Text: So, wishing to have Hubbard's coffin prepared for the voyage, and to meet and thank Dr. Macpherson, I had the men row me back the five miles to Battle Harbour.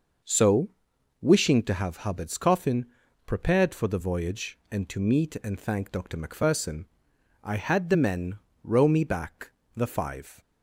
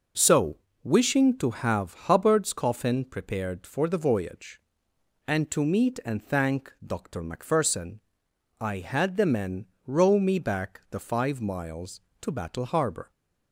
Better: second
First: pauses between "coffin" and "prepared"; at 2.8 s; 0.40 s long // pauses between "men" and "row"; slight; at 8.3 s; 0.26 s long // pauses between "back" and "the"; slight; at 9.5 s; 0.24 s long // stops before "miles to Battle Harbour"; at 10.3 s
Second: pauses between "men" and "row"; slight; at 9.6 s; 0.22 s long

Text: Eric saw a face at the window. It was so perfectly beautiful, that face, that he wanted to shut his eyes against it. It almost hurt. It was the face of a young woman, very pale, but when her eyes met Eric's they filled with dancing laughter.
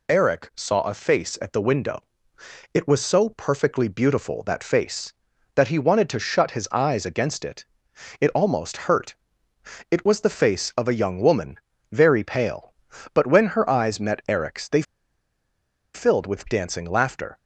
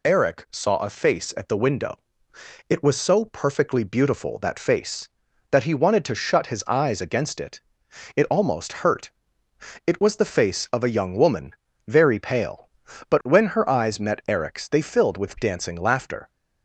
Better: second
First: pauses between "they" and "filled"; at 14.8 s; 1.1 s long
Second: none

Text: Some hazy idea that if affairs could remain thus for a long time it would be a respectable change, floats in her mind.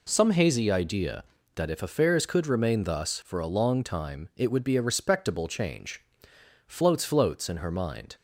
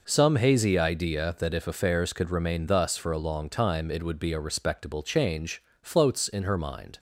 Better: second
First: says "floats" twice; at 7.0 s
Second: none

